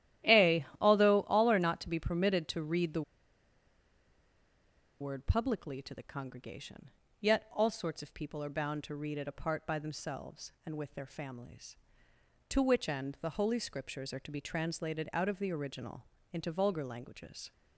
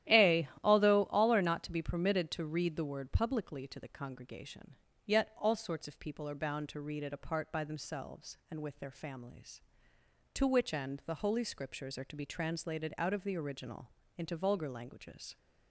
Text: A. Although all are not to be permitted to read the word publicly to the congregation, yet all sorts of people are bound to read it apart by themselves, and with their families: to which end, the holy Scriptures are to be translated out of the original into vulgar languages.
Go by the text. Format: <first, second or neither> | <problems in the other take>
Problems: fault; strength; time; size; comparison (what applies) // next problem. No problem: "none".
second | starts louder than the rest; strong; until 1.4 s; 12.5 dB; strong in the second // pauses between "the" and "word"; strong; at 3.0 s; 1.9 s long // pauses between "original" and "into"; slight; at 16.0 s; 0.26 s long; slight in the second